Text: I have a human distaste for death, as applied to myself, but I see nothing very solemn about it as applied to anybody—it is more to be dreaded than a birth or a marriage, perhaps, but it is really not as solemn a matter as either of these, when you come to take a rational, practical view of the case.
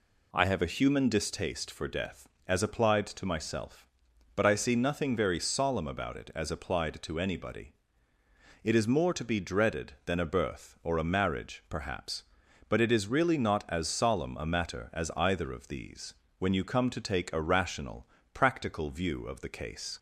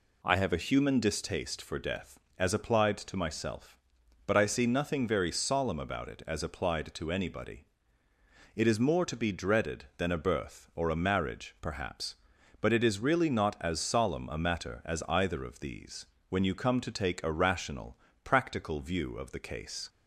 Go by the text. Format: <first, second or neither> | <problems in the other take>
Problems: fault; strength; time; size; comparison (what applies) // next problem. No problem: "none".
neither | none